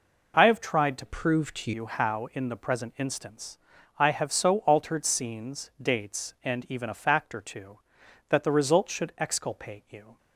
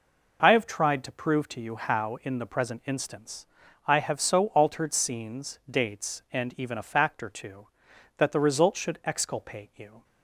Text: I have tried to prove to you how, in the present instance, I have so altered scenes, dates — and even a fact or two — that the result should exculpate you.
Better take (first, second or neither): second